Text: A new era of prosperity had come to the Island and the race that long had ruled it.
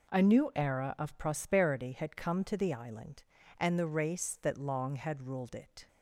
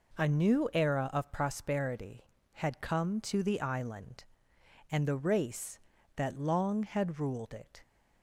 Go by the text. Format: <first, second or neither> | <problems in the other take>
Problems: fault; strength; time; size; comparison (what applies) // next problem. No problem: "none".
neither | none